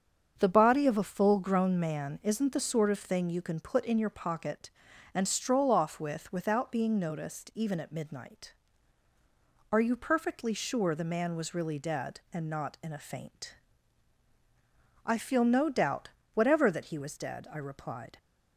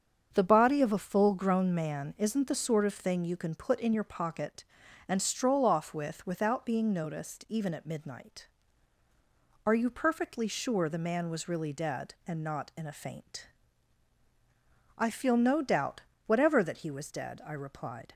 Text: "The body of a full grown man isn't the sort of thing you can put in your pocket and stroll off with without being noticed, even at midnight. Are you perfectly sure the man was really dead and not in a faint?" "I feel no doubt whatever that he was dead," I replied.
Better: neither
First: starts louder than the rest; strong; until 1.3 s; 7.5 dB // pauses between "doubt" and "whatever"; slight; at 16.0 s; 0.26 s long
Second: starts louder than the rest; strong; until 1.3 s; 7 dB // pauses between "doubt" and "whatever"; slight; at 16.0 s; 0.26 s long

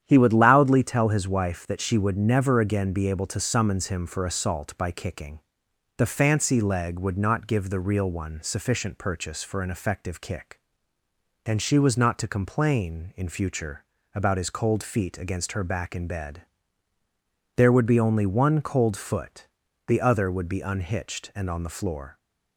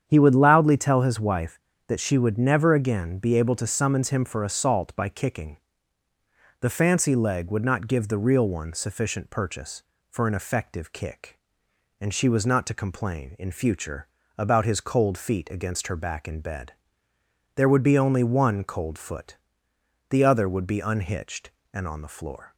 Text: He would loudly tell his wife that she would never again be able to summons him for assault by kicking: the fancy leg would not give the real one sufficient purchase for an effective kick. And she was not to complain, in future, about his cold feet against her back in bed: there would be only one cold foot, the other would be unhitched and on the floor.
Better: neither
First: starts louder than the rest; strong; until 1.0 s; 9.5 dB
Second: starts louder than the rest; strong; until 1.0 s; 8.5 dB

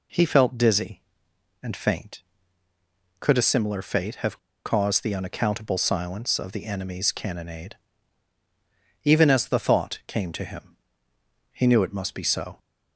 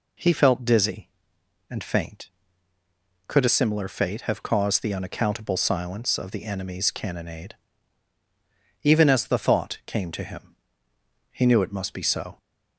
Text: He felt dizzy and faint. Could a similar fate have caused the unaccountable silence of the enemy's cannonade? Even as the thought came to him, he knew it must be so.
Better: second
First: pauses between "have" and "caused"; slight; at 4.3 s; 0.26 s long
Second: none

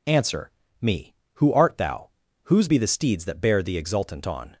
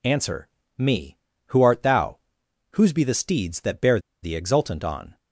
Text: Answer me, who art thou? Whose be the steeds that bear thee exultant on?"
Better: first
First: pauses between "Answer" and "me"; slight; at 0.5 s; 0.30 s long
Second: pauses between "Answer" and "me"; slight; at 0.4 s; 0.32 s long // pauses between "bear" and "thee"; slight; at 3.9 s; 0.23 s long

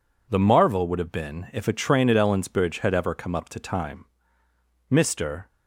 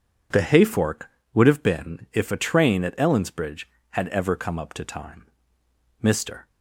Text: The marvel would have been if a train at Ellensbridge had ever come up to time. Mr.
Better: first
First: none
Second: says "hayfork" for "marvel"; at 0.3 s

